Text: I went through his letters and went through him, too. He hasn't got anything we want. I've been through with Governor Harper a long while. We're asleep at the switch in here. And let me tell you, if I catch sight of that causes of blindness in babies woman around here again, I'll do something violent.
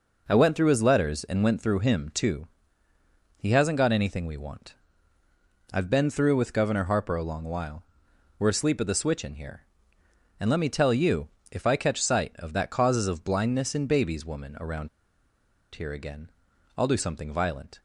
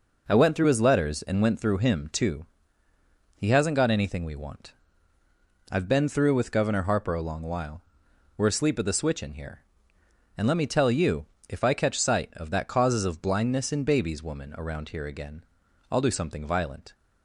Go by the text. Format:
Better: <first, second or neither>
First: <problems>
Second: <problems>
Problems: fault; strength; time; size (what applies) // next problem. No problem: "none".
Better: second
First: pauses between "around" and "here"; noticeable; at 14.8 s; 0.85 s long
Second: none